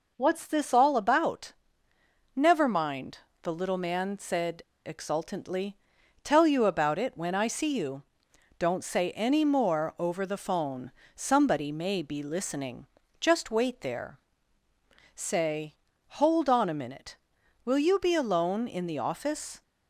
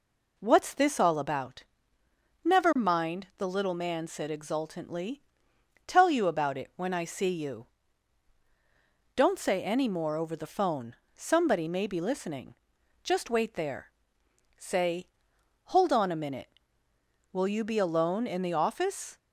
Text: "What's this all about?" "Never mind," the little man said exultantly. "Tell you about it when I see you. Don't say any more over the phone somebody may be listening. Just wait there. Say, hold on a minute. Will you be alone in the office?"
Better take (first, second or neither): second